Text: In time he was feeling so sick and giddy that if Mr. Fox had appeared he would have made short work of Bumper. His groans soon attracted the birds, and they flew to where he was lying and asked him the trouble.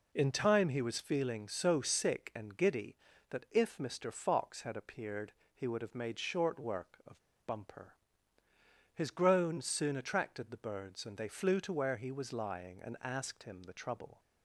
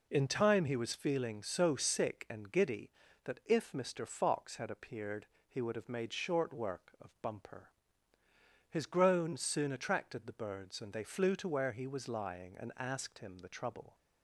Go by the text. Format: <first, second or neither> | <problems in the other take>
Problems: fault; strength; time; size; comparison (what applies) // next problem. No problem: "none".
second | pauses between "appeared" and "he"; slight; at 5.3 s; 0.22 s long; slight in the second // pauses between "of" and "Bumper"; slight; at 7.1 s; 0.30 s long